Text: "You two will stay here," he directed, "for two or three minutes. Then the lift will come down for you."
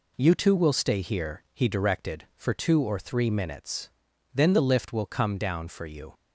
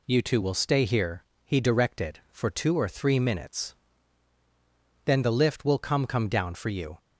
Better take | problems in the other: first | says "come" twice; at 6.0 s

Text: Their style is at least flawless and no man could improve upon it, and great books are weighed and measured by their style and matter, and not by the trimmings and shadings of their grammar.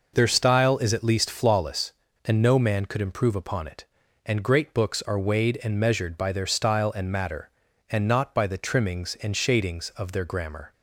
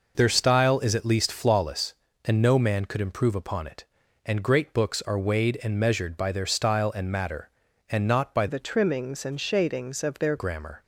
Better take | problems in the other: first | changes voice from "the" to "their"; from 8.4 to 10.3 s; 1.9 s long

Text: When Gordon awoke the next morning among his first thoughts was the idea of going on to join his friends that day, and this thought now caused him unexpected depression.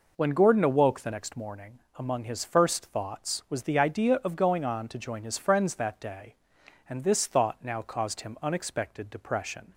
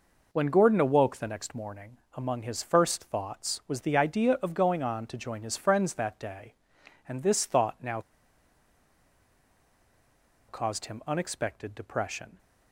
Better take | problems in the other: first | pauses between "morning" and "among"; slight; at 1.9 s; 0.16 s long; slight in the first // pauses between "now" and "caused"; strong; at 8.0 s; 2.4 s long

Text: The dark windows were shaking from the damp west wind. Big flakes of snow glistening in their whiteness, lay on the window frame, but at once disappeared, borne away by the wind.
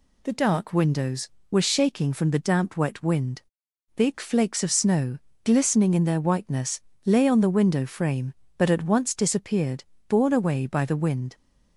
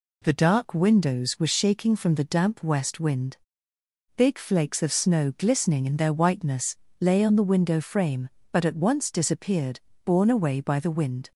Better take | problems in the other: second | says "wet" for "west"; at 2.7 s // pauses between "snow" and "glistening"; slight; at 5.1 s; 0.24 s long

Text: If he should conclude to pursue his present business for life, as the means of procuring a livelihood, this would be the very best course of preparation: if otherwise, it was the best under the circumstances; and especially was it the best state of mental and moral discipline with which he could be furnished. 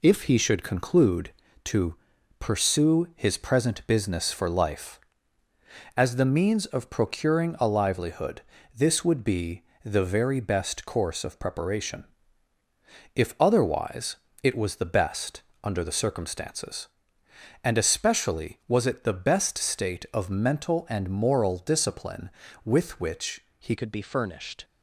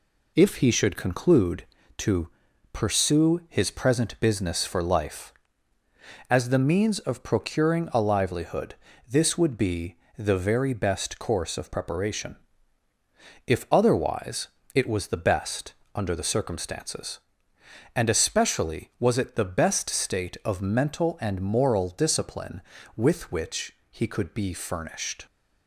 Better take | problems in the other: second | pauses between "to" and "pursue"; at 1.9 s; 0.42 s long; also in the second // pauses between "be" and "the"; slight; at 9.6 s; 0.22 s long; slight in the second // pauses between "best" and "under"; slight; at 15.4 s; 0.22 s long; slight in the second // pauses between "which" and "he"; slight; at 23.4 s; 0.18 s long; slight in the second // changes voice at "could"; from 23.7 s on; 0.9 s long

